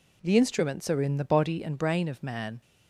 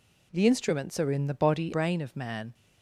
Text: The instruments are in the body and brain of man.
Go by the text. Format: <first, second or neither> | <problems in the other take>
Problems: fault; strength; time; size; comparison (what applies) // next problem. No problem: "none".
first | skips "and"; at 1.7 s